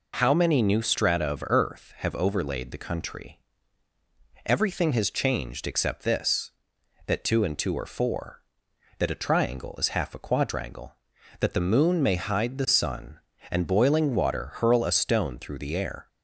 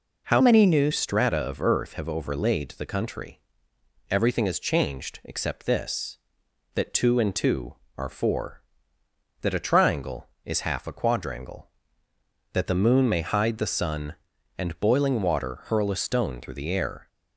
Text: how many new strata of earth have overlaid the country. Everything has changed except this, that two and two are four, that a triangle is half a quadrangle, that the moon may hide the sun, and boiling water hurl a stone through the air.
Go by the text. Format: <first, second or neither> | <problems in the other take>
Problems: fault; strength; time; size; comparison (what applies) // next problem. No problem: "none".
first | changes voice from "many" to "new"; from 0.4 to 0.9 s; 0.5 s long